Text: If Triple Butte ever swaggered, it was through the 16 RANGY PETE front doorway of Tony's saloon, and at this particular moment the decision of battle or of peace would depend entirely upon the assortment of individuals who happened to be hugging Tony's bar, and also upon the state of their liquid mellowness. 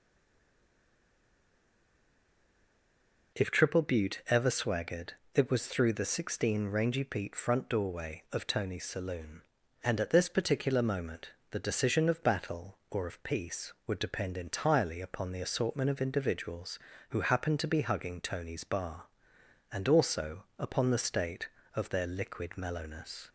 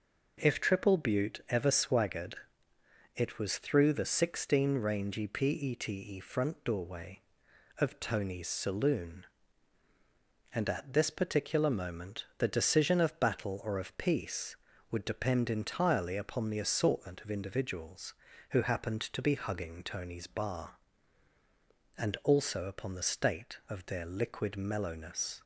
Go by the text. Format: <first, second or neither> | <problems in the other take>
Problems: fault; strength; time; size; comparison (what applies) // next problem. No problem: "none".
second | stays silent before the first word; strong; until 3.3 s; 3.3 s long // pauses between "moment" and "the"; slight; at 11.3 s; 0.22 s long // pauses between "also" and "upon"; slight; at 20.4 s; 0.16 s long